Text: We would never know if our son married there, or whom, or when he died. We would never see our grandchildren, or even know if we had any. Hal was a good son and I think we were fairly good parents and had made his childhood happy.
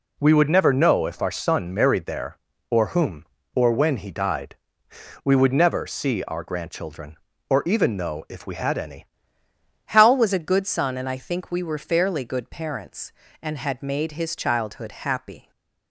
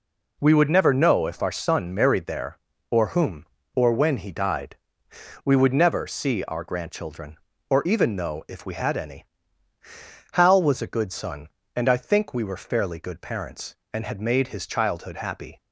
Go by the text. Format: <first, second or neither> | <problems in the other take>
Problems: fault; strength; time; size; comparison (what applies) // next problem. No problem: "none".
second | changes voice at "Hal"; from 9.8 s on; 5.7 s long // stays silent after the last word; slight; from 15.4 s on; 0.5 s long